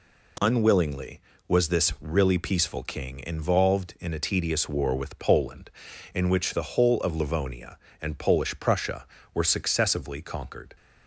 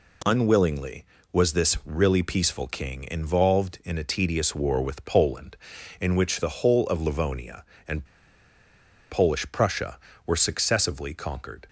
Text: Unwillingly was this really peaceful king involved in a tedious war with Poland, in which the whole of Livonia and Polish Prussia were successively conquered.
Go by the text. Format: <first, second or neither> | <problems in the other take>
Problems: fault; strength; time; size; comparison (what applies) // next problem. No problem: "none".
first | pauses between "and" and "Polish"; at 8.0 s; 1.0 s long